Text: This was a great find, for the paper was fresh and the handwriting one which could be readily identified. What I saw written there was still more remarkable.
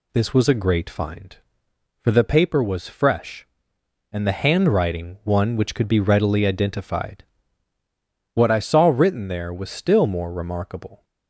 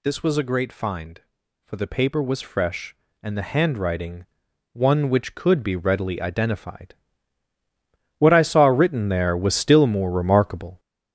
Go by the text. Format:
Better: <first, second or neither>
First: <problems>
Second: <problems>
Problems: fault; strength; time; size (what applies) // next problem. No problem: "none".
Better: first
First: none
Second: gets louder; strong; throughout; 7 dB // pauses between "handwriting" and "one"; noticeable; at 4.2 s; 0.48 s long